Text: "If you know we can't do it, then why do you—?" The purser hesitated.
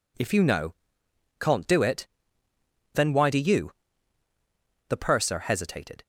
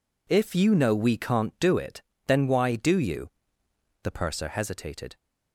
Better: second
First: skips "we"; at 1.0 s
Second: none

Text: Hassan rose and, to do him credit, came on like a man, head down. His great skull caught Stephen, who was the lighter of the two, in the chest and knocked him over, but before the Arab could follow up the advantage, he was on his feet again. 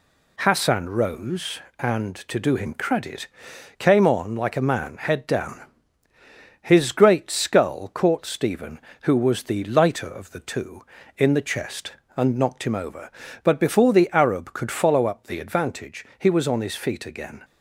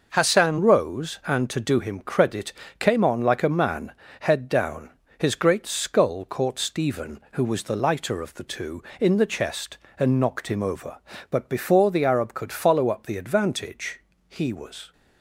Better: first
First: none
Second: stops before "on his feet again"; at 14.9 s

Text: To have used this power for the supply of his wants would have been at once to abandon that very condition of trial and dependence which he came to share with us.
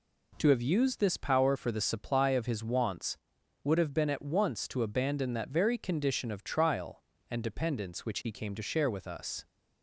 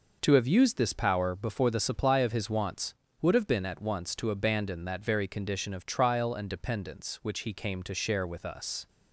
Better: first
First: none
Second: says "before" for "for"; at 1.3 s

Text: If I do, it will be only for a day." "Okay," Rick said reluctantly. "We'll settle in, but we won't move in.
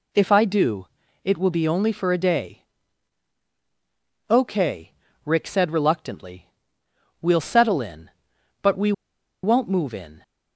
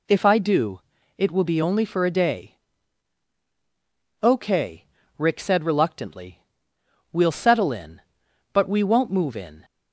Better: second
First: pauses between "we" and "won't"; noticeable; at 8.9 s; 0.51 s long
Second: none

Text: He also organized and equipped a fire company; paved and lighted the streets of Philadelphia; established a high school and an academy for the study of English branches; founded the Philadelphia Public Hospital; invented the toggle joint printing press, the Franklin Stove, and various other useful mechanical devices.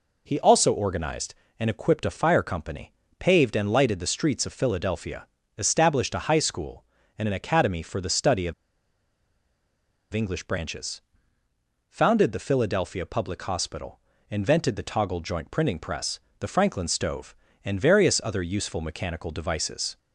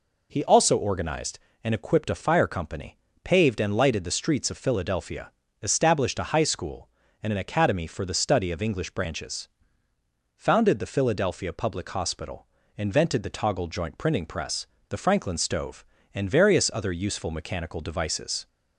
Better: second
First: pauses between "of" and "English"; strong; at 8.5 s; 1.6 s long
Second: none

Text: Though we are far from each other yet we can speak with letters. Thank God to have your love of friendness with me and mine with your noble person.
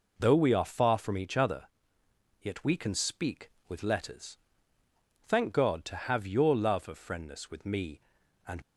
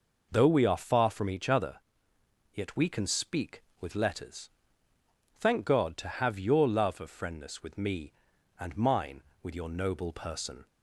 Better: second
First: pauses between "other" and "yet"; noticeable; at 1.6 s; 0.76 s long // stops before "mine with your noble person"; at 8.6 s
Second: pauses between "other" and "yet"; noticeable; at 1.7 s; 0.76 s long

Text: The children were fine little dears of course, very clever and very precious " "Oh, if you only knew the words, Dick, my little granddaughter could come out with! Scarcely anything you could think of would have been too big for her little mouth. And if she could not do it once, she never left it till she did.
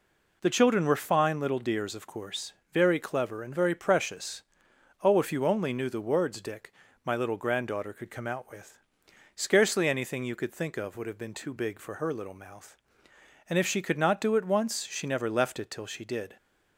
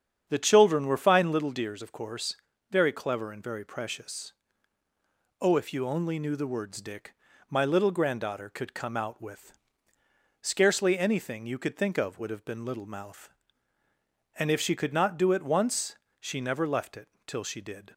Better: first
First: none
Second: starts louder than the rest; strong; until 1.3 s; 10 dB // skips "too big for her"; at 12.6 s // pauses between "it" and "till"; slight; at 17.0 s; 0.18 s long

